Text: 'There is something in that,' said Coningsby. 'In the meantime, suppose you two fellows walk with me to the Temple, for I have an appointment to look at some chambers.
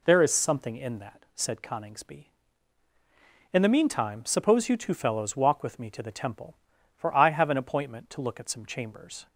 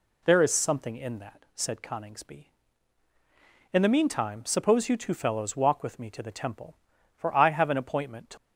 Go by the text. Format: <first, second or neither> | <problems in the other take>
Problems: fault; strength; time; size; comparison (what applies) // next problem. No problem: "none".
first | stops before "look at some chambers"; at 8.3 s